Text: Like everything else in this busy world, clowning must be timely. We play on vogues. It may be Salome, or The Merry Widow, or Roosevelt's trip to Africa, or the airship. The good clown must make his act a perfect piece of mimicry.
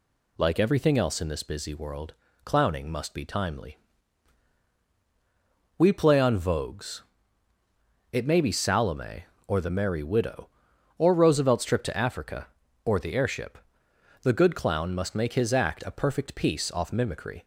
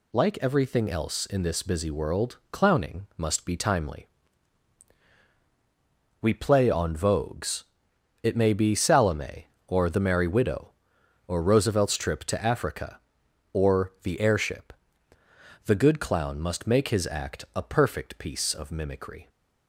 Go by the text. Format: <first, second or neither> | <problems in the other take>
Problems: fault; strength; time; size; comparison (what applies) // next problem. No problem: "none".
second | says "off" for "of"; at 16.6 s